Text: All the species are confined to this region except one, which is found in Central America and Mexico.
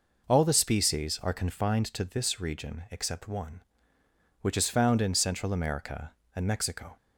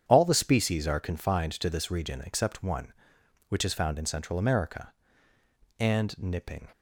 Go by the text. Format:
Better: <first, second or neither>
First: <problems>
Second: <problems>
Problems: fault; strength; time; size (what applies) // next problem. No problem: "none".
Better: first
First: none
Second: starts louder than the rest; strong; until 1.0 s; 8.5 dB // says "Nipping" for "Mexico"; at 6.1 s